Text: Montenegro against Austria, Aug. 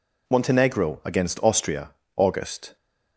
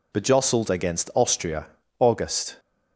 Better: first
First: none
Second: says "Bejostled" for "Montenegro"; at 0.1 s

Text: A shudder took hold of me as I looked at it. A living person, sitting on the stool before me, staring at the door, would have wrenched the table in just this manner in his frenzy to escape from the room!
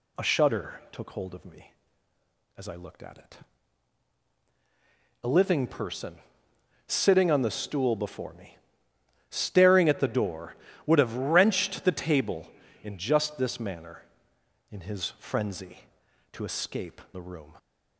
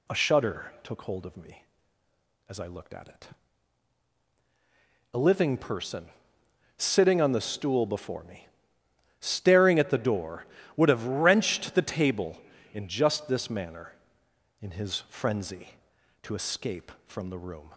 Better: second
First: skips "from"; at 17.0 s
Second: none

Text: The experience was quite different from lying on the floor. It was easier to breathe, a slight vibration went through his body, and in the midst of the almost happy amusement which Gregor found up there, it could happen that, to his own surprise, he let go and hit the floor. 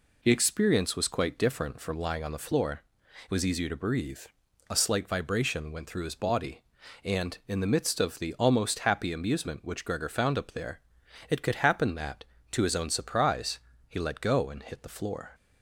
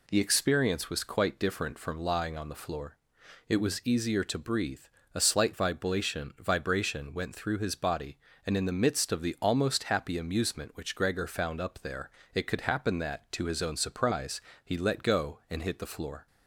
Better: first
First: none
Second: says "vibration" twice; at 6.3 s

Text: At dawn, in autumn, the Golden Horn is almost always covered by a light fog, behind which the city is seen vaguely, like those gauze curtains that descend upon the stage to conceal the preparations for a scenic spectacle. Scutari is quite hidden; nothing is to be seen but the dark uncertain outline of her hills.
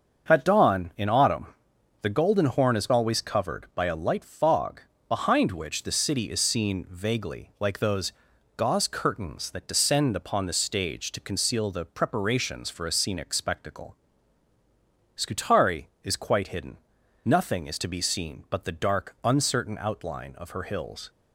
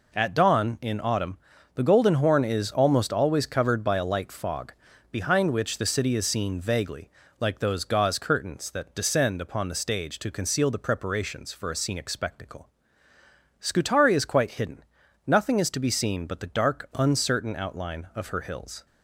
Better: second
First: starts louder than the rest; until 1.3 s; 6.5 dB // skips "almost"; at 2.9 s // pauses between "those" and "gauze"; at 8.1 s; 0.44 s long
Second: none

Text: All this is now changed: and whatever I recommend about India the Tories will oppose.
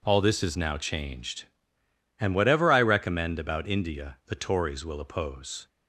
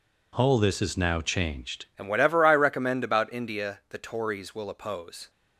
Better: first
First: none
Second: changes voice at "and"; from 1.9 s on; 3.3 s long

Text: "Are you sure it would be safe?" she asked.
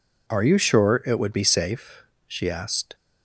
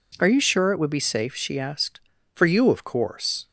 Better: first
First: none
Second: goes on to say "For you of course"; noticeable; from 2.3 s on; 1.1 s long

